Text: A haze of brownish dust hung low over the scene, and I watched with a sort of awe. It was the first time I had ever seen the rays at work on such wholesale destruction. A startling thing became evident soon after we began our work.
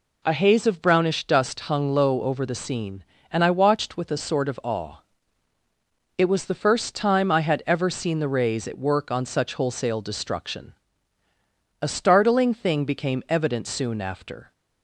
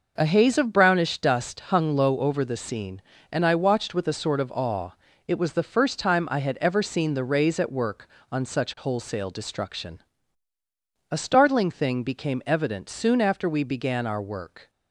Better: second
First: stops before "we began our work"; at 14.5 s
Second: none

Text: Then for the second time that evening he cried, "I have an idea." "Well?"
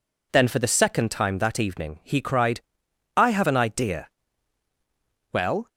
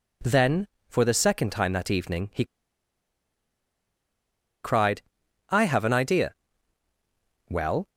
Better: first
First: none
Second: pauses between "he" and "cried"; strong; at 2.4 s; 2.1 s long

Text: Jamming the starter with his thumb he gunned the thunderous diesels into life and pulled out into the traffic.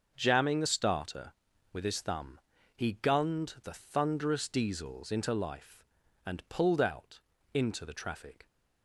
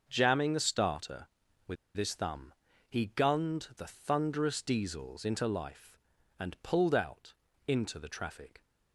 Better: first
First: starts louder than the rest; until 1.1 s; 6.5 dB // pauses between "thumb" and "he"; at 2.3 s; 0.38 s long // pauses between "out" and "into"; slight; at 7.1 s; 0.34 s long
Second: starts louder than the rest; until 1.0 s; 7 dB // pauses between "with" and "his"; slight; at 1.7 s; 0.21 s long // pauses between "thumb" and "he"; at 2.5 s; 0.38 s long // pauses between "out" and "into"; slight; at 7.3 s; 0.34 s long

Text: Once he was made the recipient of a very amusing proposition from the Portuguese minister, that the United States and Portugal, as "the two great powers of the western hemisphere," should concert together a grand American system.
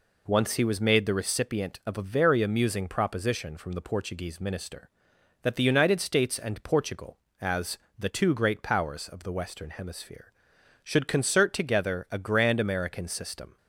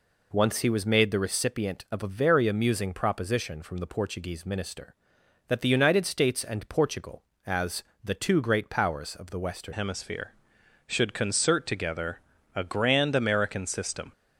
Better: first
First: pauses between "as" and "the"; slight; at 7.7 s; 0.18 s long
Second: pauses between "as" and "the"; slight; at 7.8 s; 0.18 s long // changes voice at "hemisphere"; from 9.7 s on; 4.4 s long // pauses between "together" and "a"; slight; at 12.2 s; 0.36 s long

